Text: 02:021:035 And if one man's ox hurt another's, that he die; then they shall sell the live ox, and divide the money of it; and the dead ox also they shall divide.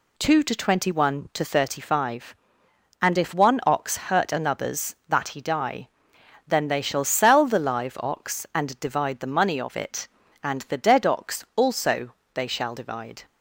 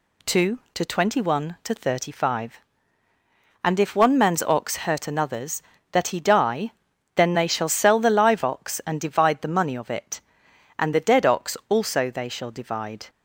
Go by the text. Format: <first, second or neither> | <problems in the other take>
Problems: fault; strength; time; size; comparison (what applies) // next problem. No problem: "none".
second | skips "man's"; at 3.6 s // pauses between "also" and "they"; slight; at 12.1 s; 0.22 s long